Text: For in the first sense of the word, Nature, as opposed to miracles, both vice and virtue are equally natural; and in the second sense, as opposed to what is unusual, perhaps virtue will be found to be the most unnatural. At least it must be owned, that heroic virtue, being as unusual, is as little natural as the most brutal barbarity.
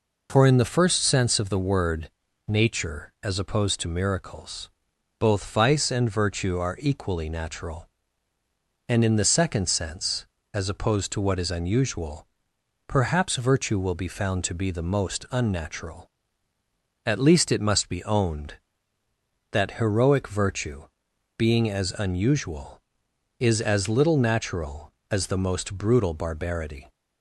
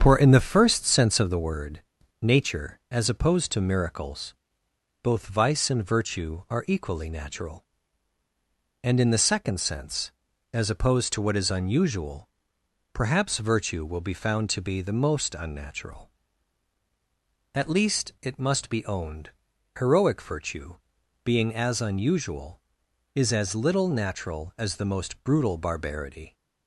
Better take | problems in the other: first | starts louder than the rest; strong; until 1.0 s; 7.5 dB // skips "that"; at 19.5 s

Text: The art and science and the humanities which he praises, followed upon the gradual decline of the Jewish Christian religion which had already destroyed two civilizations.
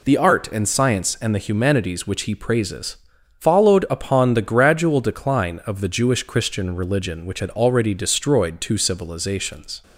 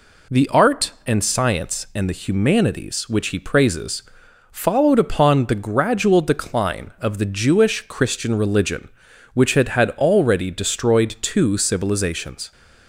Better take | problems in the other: first | says "had" twice; at 9.6 s

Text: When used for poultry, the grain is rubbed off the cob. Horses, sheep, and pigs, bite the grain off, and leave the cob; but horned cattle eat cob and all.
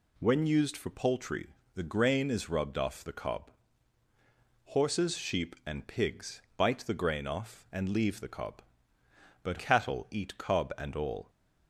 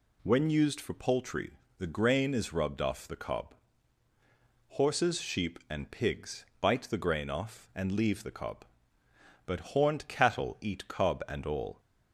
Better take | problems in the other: second | skips "horned"; at 9.5 s

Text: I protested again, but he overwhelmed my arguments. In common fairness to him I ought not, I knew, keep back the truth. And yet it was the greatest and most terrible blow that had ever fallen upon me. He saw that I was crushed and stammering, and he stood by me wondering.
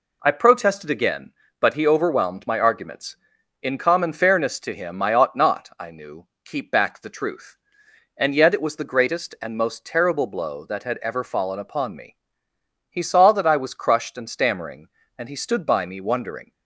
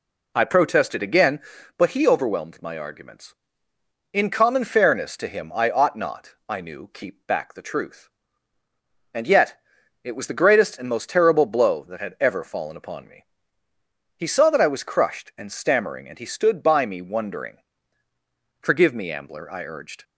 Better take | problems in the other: first | pauses between "yet" and "it"; at 9.5 s; 0.44 s long // goes on to say "Forgive me Ambler I urged"; from 18.6 s on; 1.4 s long

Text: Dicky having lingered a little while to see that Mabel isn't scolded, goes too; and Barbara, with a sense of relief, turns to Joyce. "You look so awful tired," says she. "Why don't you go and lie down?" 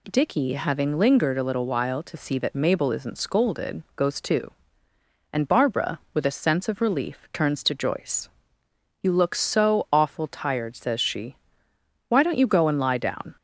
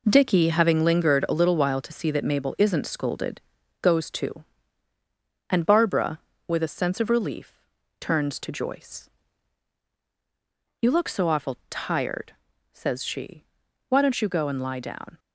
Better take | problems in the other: first | gets quieter; strong; throughout; 8 dB

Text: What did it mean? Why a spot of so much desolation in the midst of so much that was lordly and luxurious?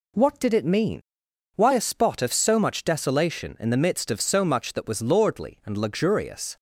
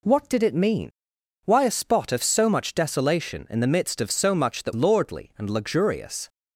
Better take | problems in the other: first | skips "was"; at 4.7 s

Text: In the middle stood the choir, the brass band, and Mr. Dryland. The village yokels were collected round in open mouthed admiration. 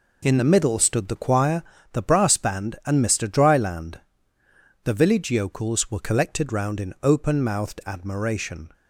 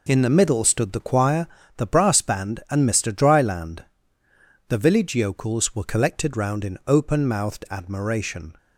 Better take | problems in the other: neither | none

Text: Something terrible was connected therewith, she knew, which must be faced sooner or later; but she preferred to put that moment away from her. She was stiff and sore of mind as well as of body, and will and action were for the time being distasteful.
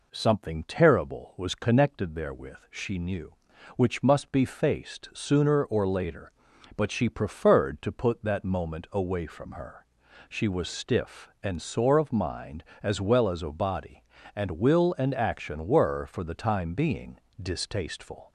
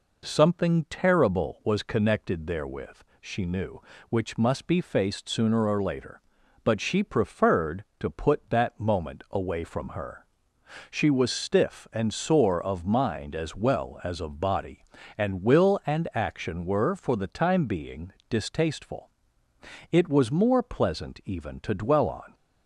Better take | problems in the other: first | pauses between "being" and "distasteful"; slight; at 18.1 s; 0.16 s long; slight in the first // goes on to say "It was more pleasant even to dwell on"; strong; from 19.9 s on; 2.4 s long

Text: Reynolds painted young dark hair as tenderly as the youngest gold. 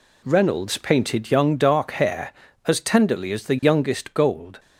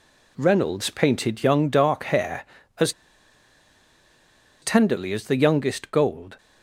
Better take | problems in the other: first | pauses between "as" and "tenderly"; strong; at 2.9 s; 1.7 s long

